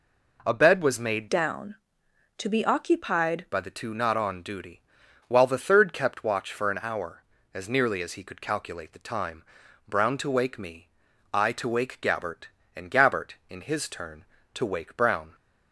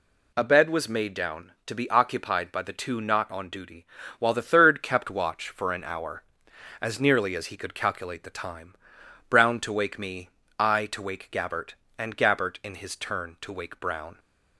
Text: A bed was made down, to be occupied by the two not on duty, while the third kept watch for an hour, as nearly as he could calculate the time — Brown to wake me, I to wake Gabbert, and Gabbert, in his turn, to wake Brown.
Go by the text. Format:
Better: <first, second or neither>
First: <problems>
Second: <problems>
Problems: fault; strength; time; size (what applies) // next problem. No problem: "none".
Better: second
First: changes voice from "down" to "occupied"; from 1.2 to 3.4 s; 2.2 s long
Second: none